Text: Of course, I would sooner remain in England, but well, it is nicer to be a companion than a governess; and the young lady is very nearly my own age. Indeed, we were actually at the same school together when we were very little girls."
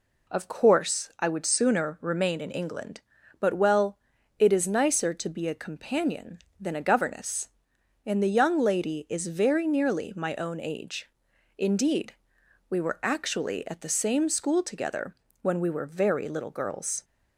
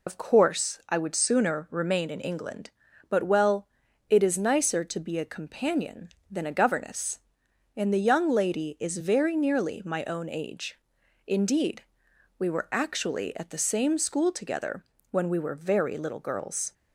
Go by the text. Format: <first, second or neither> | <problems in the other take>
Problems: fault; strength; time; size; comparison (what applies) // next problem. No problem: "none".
first | loses the start of "Of"; at 0.0 s; 80 ms // pauses between "together" and "when"; slight; at 14.8 s; 0.28 s long; slight in the first